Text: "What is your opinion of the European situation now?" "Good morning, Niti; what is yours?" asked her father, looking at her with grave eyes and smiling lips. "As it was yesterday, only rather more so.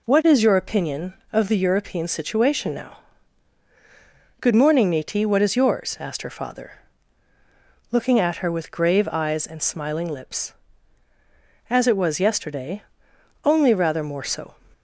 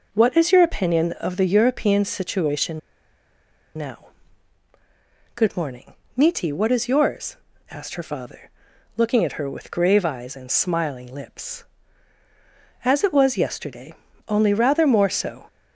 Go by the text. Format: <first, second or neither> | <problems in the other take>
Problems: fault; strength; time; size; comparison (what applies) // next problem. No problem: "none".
first | pauses between "situation" and "now"; at 2.7 s; 0.98 s long